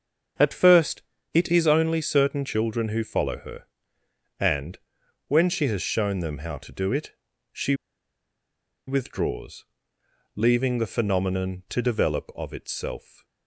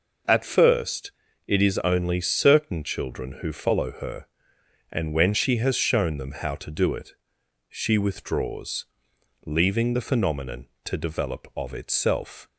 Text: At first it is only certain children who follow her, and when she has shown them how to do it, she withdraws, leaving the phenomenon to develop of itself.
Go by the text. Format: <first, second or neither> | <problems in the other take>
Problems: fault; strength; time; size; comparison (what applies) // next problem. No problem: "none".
second | starts louder than the rest; until 1.7 s; 6.5 dB // pauses between "first" and "it"; slight; at 1.0 s; 0.32 s long; slight in the second // pauses between "and" and "when"; noticeable; at 4.7 s; 0.50 s long // pauses between "she" and "withdraws"; at 7.7 s; 1.1 s long